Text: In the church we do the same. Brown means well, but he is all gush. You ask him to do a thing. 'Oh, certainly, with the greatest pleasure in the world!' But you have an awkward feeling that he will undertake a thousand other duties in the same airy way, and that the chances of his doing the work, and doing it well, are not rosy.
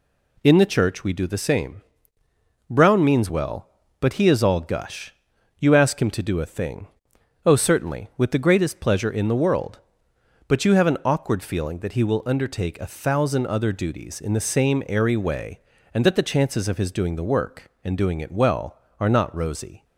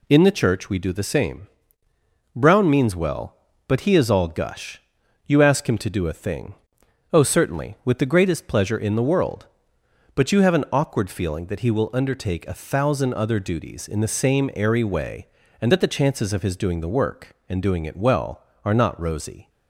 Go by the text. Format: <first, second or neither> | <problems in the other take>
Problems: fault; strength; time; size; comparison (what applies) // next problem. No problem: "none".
neither | none